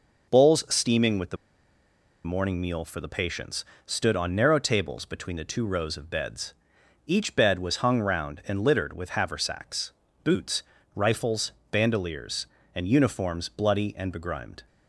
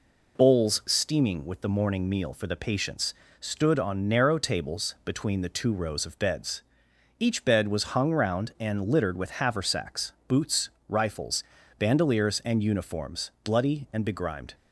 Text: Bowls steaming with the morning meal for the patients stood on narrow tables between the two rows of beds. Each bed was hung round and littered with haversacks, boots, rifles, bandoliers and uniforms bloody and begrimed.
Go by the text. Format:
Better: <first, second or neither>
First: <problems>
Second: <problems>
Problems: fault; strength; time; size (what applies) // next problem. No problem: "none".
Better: second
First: pauses between "the" and "morning"; noticeable; at 1.3 s; 0.89 s long // pauses between "patients" and "stood"; slight; at 3.6 s; 0.22 s long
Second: pauses between "patients" and "stood"; slight; at 3.1 s; 0.26 s long